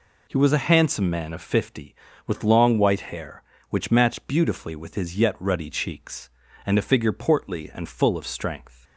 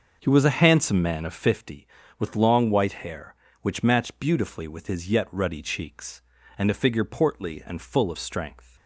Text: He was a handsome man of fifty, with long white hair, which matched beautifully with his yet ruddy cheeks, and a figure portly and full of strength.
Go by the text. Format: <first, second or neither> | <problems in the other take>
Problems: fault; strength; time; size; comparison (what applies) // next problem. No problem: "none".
first | starts louder than the rest; until 1.6 s; 6.5 dB